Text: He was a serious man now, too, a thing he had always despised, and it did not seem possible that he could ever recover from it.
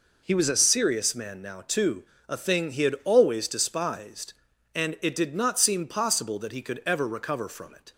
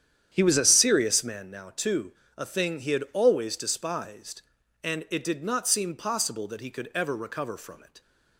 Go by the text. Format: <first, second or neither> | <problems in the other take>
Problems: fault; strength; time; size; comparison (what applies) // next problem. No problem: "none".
first | starts louder than the rest; strong; until 1.4 s; 9.5 dB